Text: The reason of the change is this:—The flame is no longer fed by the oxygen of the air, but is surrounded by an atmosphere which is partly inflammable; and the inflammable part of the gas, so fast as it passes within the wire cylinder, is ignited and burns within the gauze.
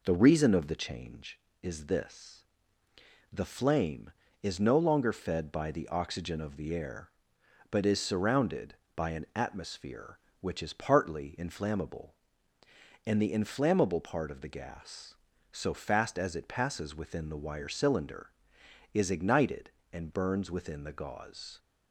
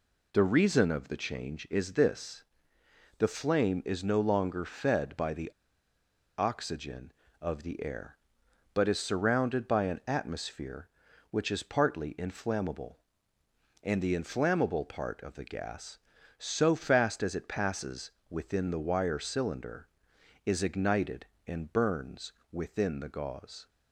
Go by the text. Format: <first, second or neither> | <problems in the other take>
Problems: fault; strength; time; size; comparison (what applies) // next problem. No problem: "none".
first | pauses between "the" and "oxygen"; noticeable; at 5.5 s; 0.86 s long // pauses between "passes" and "within"; slight; at 18.1 s; 0.18 s long // pauses between "burns" and "within"; slight; at 22.3 s; 0.18 s long